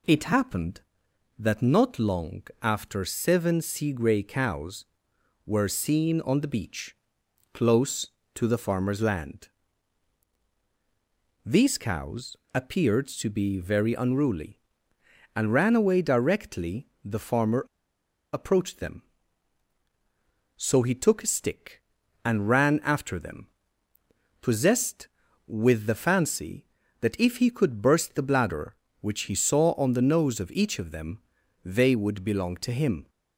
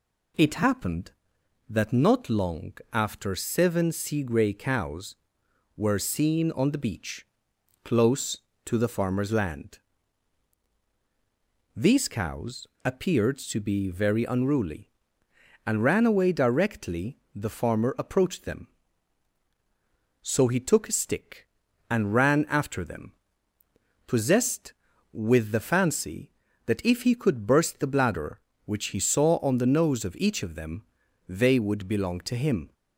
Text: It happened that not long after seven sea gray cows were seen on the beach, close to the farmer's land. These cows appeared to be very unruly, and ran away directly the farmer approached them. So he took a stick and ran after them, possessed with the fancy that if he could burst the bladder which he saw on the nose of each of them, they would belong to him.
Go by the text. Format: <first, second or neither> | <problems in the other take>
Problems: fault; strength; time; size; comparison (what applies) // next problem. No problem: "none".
second | pauses between "long" and "after"; slight; at 2.4 s; 0.20 s long; slight in the second // pauses between "cows" and "appeared"; slight; at 12.3 s; 0.18 s long; slight in the second // pauses between "directly" and "the"; slight; at 16.8 s; 0.18 s long; slight in the second // pauses between "farmer" and "approached"; noticeable; at 17.6 s; 0.68 s long